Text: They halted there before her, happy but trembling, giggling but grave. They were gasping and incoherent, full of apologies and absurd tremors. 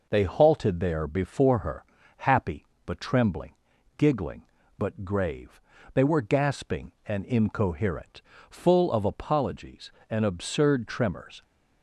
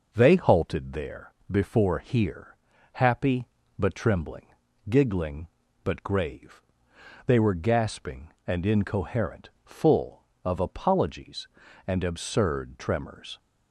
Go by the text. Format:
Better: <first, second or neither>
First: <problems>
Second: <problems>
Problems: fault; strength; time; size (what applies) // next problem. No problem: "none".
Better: first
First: none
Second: pauses between "there" and "before"; slight; at 1.3 s; 0.18 s long // says "here" for "her"; at 1.9 s